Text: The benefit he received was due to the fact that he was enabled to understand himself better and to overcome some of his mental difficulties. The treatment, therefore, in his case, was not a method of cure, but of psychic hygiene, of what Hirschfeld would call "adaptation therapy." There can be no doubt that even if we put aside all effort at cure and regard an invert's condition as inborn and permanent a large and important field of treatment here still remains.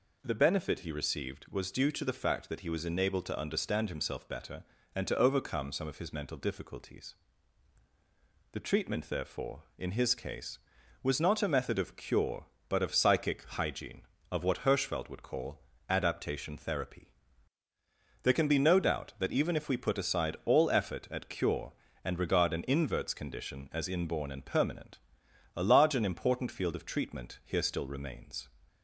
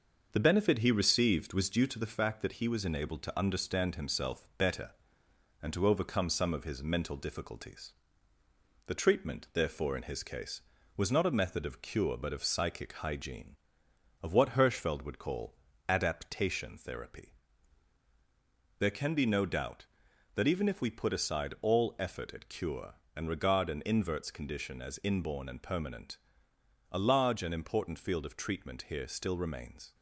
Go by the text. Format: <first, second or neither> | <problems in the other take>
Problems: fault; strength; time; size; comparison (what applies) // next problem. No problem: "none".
first | gets quieter; noticeable; throughout; 4 dB // pauses between "call" and "adaptation"; slight; at 15.5 s; 0.32 s long; slight in the first // pauses between "permanent" and "a"; noticeable; at 26.1 s; 0.74 s long; noticeable in the first